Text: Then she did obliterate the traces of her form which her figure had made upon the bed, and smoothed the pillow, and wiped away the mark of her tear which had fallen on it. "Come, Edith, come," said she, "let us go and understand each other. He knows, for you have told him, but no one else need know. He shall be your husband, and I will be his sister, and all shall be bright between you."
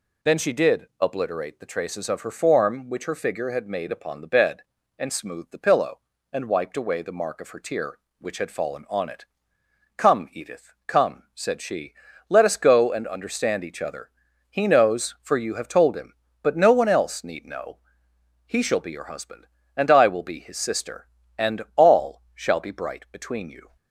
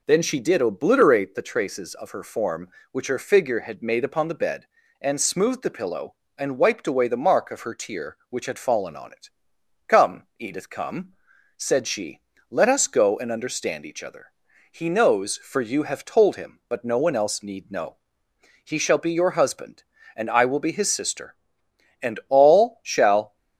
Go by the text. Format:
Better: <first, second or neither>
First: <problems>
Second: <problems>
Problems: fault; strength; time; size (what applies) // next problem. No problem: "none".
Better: first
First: none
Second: stops before "be bright between you"; at 23.3 s